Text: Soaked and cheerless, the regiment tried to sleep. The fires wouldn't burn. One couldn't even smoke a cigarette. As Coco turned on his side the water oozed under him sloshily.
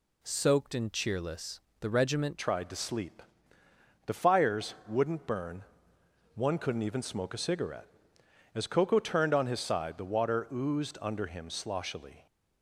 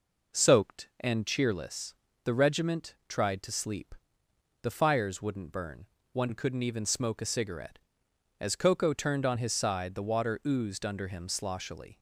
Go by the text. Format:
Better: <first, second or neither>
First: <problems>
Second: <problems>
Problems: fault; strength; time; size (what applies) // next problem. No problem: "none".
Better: second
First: changes voice at "tried"; from 2.3 s on; 9.9 s long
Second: none